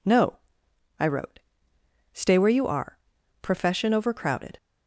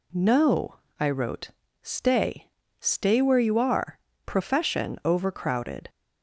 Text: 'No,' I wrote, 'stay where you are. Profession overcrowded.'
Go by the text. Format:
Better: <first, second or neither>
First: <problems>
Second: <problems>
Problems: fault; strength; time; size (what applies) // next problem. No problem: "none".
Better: first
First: none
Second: says "stay" twice; at 2.7 s